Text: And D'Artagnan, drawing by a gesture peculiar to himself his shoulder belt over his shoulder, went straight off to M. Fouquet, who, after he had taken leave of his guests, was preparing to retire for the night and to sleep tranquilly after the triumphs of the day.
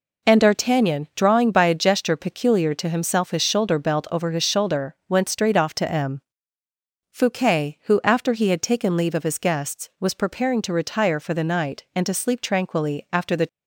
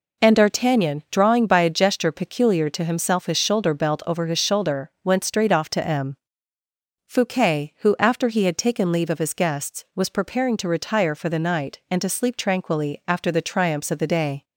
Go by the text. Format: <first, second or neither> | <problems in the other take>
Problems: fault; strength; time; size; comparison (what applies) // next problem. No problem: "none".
second | stops before "triumphs of the day"; at 13.4 s